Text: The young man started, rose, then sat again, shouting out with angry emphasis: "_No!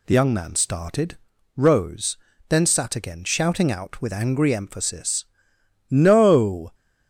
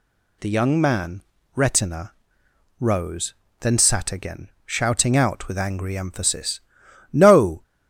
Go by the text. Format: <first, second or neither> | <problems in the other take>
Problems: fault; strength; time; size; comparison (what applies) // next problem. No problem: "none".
first | says "retina" for "started"; at 1.5 s